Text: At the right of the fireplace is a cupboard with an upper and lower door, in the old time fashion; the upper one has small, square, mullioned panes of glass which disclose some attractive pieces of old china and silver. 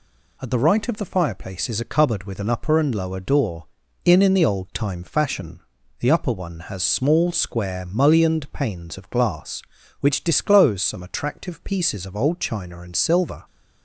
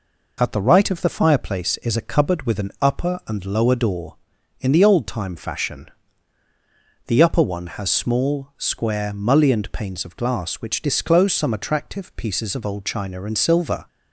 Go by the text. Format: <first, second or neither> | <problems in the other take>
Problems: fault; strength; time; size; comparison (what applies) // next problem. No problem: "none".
second | says "in" twice; at 4.2 s